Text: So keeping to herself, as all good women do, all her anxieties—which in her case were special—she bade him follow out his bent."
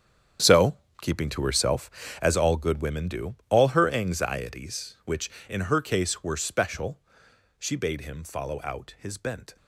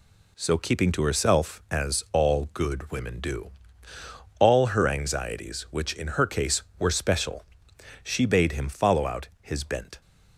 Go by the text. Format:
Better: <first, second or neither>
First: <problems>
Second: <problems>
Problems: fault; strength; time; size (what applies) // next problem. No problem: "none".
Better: second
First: gets quieter; strong; throughout; 13 dB // pauses between "So" and "keeping"; slight; at 0.7 s; 0.26 s long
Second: none